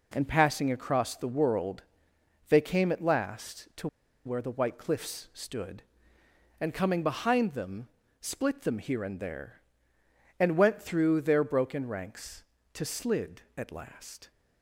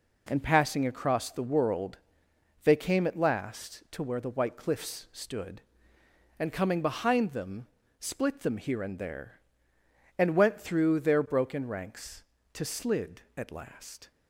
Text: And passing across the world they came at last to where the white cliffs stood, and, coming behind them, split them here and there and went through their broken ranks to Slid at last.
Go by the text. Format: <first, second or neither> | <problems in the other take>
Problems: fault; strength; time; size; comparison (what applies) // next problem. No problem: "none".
second | pauses between "world" and "they"; noticeable; at 1.8 s; 0.66 s long; noticeable in the second // pauses between "to" and "where"; at 3.8 s; 0.37 s long